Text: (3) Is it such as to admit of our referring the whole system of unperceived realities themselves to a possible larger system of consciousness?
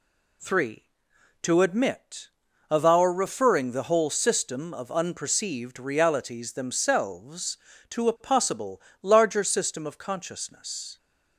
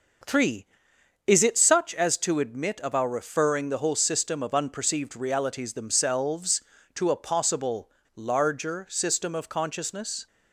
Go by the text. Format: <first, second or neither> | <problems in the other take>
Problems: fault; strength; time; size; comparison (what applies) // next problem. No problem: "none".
second | skips "Is it such as"; at 1.1 s // pauses between "possible" and "larger"; slight; at 8.8 s; 0.20 s long; slight in the second